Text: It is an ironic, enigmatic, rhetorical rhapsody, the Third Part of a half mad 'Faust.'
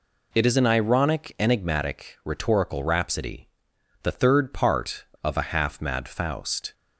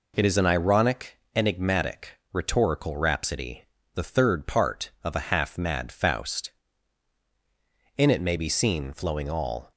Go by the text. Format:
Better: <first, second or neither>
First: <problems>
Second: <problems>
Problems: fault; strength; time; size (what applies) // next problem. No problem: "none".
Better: first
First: none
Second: goes on to say "In it may be seen flowing all"; strong; from 7.9 s on; 1.7 s long